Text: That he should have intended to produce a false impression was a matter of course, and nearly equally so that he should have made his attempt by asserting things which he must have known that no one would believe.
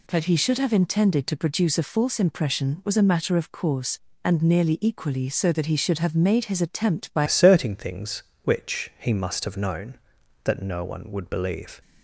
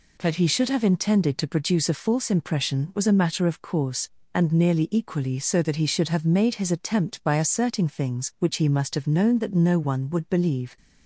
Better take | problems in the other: second | changes voice at "asserting"; from 7.2 s on; 4.6 s long

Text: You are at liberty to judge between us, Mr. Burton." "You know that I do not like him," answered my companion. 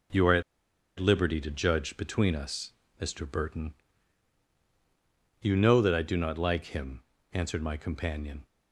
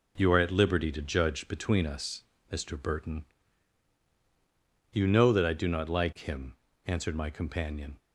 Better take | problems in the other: second | pauses between "at" and "liberty"; noticeable; at 0.4 s; 0.56 s long

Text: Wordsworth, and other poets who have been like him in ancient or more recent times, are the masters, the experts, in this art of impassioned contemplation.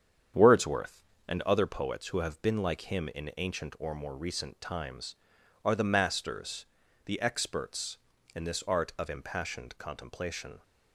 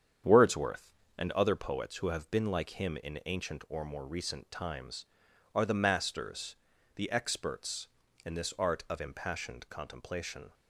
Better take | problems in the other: neither | starts louder than the rest; strong; the same in both

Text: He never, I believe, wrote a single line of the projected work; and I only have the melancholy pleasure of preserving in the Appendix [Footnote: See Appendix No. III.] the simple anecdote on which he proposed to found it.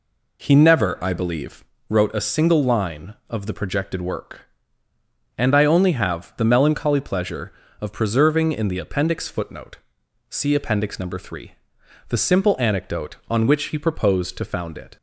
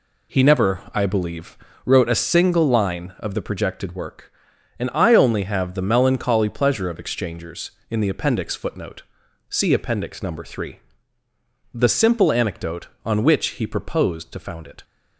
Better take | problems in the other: first | says "exchangers" for "preserving"; at 6.9 s

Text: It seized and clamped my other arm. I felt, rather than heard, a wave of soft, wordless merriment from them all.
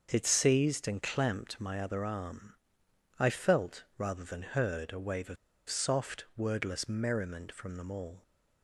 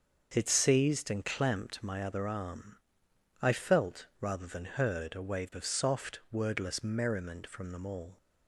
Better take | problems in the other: second | starts louder than the rest; until 1.1 s; 6.5 dB; also in the second // pauses between "of" and "soft"; slight; at 5.3 s; 0.32 s long

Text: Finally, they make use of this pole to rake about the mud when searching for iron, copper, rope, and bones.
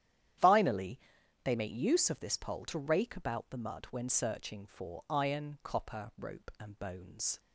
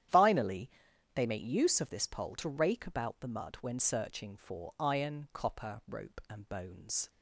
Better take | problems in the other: neither | starts louder than the rest; strong; the same in both

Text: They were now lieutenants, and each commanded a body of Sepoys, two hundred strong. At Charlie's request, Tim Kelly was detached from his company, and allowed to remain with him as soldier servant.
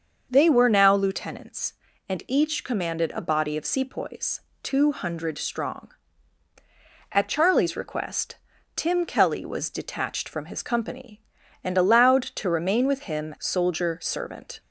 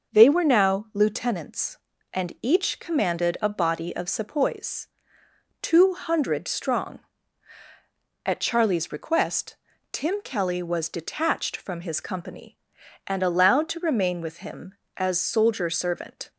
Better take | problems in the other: second | starts louder than the rest; until 1.3 s; 6.5 dB // skips "as"; at 13.3 s

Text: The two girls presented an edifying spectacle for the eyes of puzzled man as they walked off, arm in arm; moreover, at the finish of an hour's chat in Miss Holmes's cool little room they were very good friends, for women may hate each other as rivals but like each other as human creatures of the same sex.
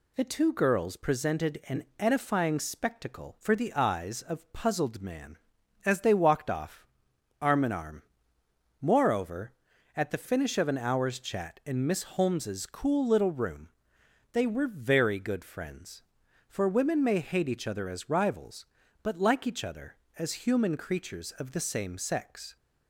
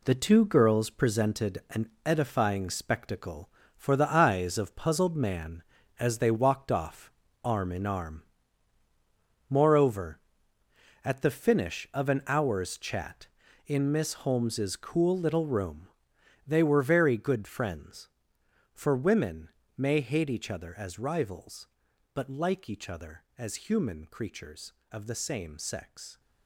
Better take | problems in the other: first | gets quieter; strong; throughout; 8 dB // pauses between "an" and "edifying"; slight; at 1.8 s; 0.18 s long // pauses between "room" and "they"; noticeable; at 15.8 s; 0.60 s long; noticeable in the first // pauses between "women" and "may"; slight; at 19.4 s; 0.26 s long

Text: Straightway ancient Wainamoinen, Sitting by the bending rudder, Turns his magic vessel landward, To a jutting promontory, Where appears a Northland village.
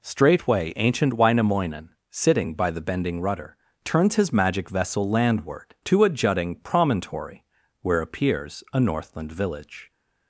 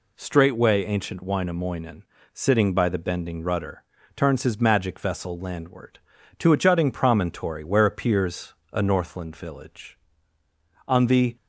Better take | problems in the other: first | pauses between "appears" and "a"; slight; at 8.5 s; 0.18 s long // goes on to say "On the"; slight; from 10.8 s on; 0.48 s long

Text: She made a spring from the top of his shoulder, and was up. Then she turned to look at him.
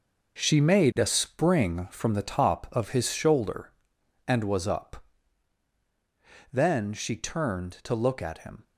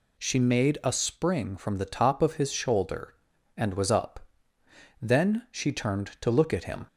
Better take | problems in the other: second | gets quieter; strong; throughout; 9.5 dB

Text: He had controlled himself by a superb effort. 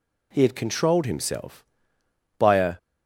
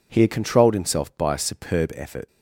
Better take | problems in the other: second | stops before "superb effort"; at 2.7 s

